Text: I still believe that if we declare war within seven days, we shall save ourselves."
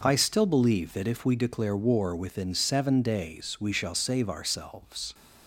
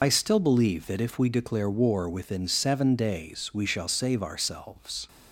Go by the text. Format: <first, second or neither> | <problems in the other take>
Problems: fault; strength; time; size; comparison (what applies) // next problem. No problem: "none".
first | loses the start of "I"; at 0.0 s; 75 ms